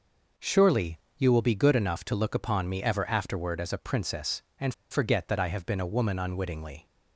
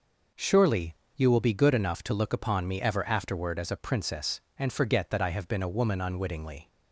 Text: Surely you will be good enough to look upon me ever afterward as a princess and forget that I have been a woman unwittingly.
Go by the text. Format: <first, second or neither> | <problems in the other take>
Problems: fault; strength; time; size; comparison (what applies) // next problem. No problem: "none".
second | pauses between "Surely" and "you"; slight; at 0.9 s; 0.18 s long; slight in the second // pauses between "and" and "forget"; slight; at 4.7 s; 0.16 s long